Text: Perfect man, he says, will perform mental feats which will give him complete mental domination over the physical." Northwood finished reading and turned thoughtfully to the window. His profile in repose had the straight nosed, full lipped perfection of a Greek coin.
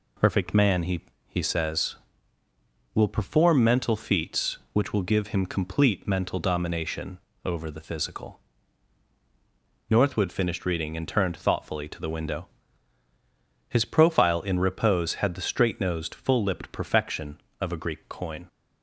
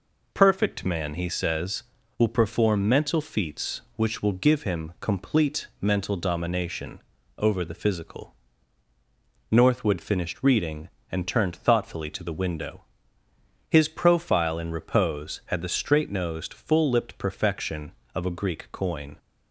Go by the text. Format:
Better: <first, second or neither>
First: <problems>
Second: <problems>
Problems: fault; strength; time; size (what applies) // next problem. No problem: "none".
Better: second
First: says "he" twice; at 1.2 s // pauses between "domination" and "over"; slight; at 7.1 s; 0.26 s long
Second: pauses between "domination" and "over"; slight; at 7.0 s; 0.36 s long